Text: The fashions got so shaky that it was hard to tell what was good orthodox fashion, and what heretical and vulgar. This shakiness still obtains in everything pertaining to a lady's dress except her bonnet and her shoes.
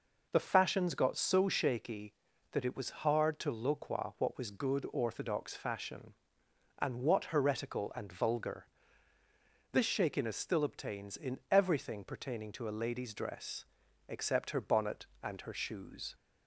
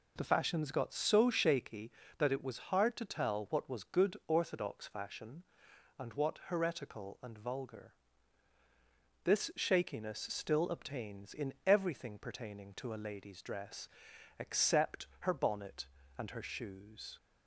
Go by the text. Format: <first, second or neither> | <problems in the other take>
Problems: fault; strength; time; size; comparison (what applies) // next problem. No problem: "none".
second | says "loqua" for "tell"; at 3.5 s // pauses between "dress" and "except"; noticeable; at 13.6 s; 0.46 s long; noticeable in the second